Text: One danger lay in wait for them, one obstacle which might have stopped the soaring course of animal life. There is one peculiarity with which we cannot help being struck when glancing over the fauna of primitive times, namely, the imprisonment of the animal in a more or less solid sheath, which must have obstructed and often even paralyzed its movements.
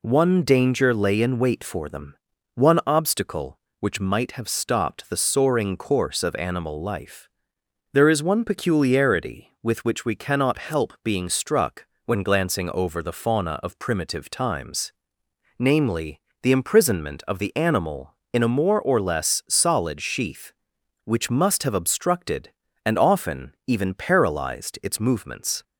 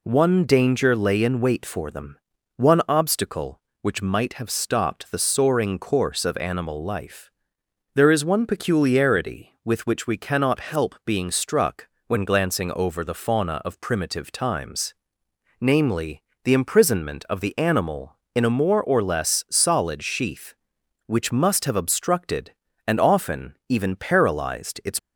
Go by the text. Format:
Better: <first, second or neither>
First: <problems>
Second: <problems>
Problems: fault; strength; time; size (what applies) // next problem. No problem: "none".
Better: first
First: pauses between "struck" and "when"; slight; at 11.8 s; 0.22 s long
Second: pauses between "struck" and "when"; slight; at 11.8 s; 0.22 s long // stops before "movements"; at 24.9 s